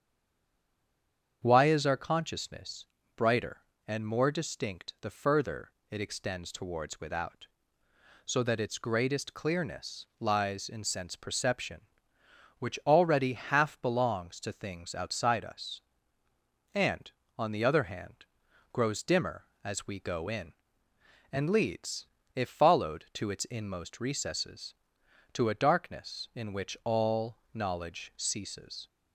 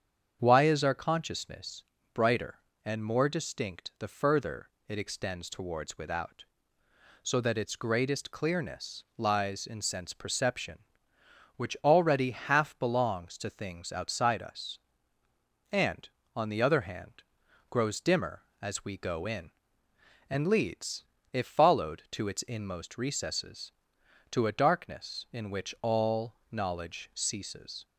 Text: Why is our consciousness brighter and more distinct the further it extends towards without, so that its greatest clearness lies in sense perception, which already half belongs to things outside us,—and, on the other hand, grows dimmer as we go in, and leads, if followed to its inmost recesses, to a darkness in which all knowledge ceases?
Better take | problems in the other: second | stays silent before the first word; noticeable; until 1.4 s; 1.4 s long // starts louder than the rest; strong; until 2.4 s; 7.5 dB; strong in the second // pauses between "consciousness" and "brighter"; slight; at 2.8 s; 0.32 s long; slight in the second // pauses between "further" and "it"; slight; at 5.7 s; 0.18 s long; slight in the second // pauses between "all" and "knowledge"; slight; at 27.3 s; 0.18 s long; slight in the second

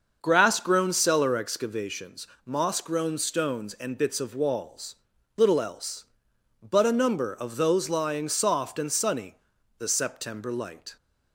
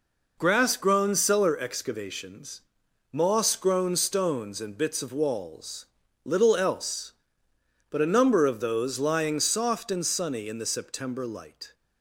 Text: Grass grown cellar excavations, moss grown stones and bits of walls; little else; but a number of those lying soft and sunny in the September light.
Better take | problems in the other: second | starts louder than the rest; until 1.2 s; 6.5 dB // skips "in"; at 9.5 s

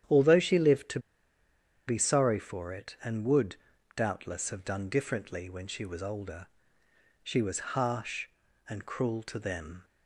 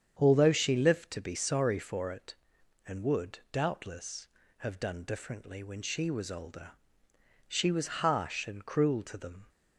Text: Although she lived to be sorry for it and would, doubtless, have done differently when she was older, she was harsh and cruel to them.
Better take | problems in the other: second | starts louder than the rest; strong; until 2.0 s; 9.5 dB; strong in the second // pauses between "to" and "be"; noticeable; at 0.9 s; 0.89 s long

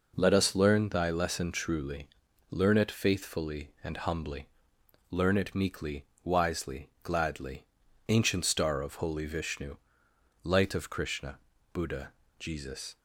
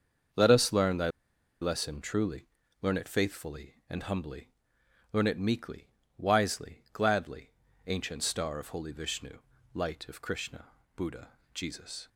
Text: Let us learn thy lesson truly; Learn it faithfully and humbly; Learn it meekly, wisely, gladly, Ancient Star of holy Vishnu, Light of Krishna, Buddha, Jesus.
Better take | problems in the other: first | starts louder than the rest; until 1.8 s; 6.5 dB // pauses between "thy" and "lesson"; noticeable; at 1.0 s; 0.51 s long

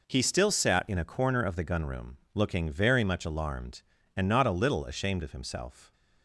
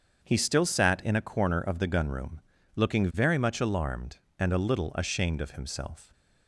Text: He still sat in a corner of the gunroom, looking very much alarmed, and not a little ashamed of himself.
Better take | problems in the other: first | starts louder than the rest; until 1.2 s; 7 dB // skips "not"; at 4.5 s

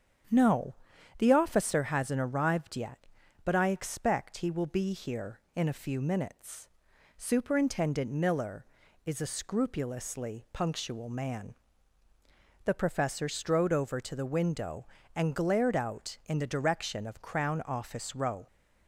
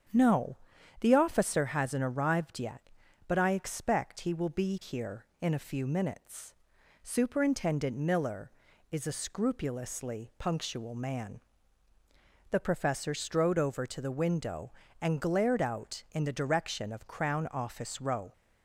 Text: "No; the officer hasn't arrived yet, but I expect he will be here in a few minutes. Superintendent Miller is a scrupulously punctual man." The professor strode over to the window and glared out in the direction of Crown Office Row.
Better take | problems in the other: neither | starts louder than the rest; strong; the same in both

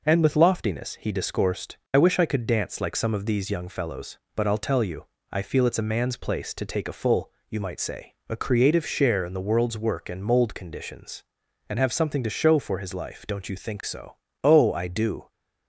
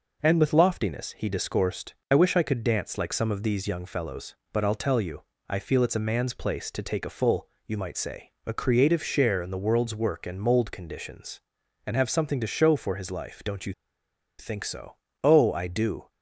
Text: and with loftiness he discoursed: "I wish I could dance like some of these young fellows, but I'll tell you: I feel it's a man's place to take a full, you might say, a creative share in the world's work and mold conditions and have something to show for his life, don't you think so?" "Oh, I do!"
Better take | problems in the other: first | pauses between "you" and "think"; noticeable; at 13.7 s; 0.67 s long

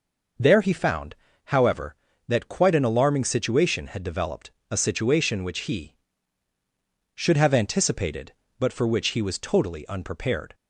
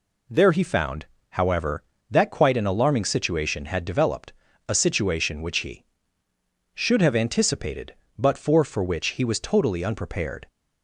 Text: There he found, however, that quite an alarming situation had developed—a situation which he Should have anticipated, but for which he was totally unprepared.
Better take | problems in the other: first | says "for" twice; at 8.6 s

